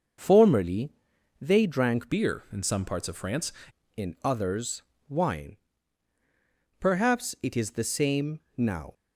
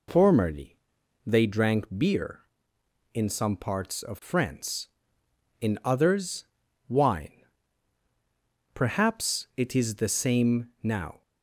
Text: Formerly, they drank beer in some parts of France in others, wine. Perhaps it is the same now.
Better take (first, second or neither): second